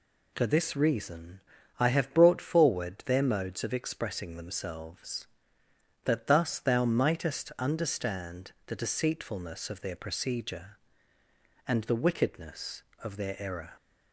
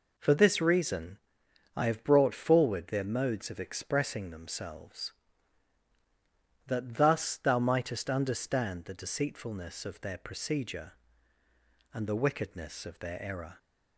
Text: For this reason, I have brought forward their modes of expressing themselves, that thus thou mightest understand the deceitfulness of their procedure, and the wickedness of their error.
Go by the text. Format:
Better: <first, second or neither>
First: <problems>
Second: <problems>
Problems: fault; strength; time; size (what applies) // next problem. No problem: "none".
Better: neither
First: none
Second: none